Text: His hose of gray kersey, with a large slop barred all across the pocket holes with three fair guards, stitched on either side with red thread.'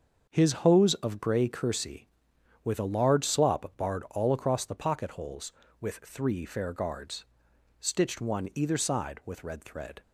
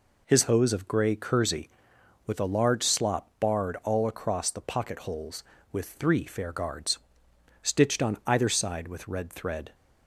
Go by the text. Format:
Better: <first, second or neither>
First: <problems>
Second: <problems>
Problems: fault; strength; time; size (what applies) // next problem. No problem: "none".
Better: second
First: starts louder than the rest; until 1.3 s; 6.5 dB // says "one" for "on"; at 8.1 s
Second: none